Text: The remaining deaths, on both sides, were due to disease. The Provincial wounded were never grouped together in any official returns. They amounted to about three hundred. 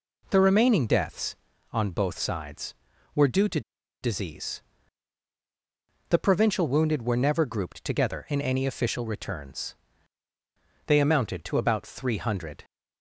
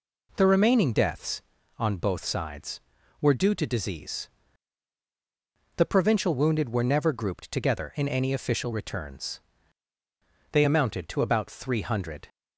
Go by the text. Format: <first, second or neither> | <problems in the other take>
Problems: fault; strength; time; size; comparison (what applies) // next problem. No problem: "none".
second | pauses between "to" and "disease"; at 3.6 s; 0.42 s long